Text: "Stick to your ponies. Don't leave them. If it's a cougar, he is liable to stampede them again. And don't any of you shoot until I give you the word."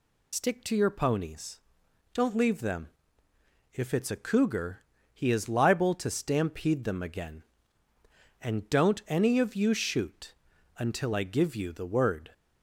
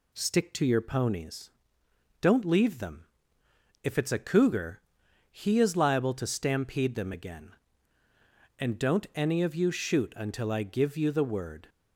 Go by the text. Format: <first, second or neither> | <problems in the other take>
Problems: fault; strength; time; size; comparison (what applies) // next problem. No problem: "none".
second | loses the start of "Stick"; at 0.3 s; 60 ms // pauses between "shoot" and "until"; at 10.3 s; 0.44 s long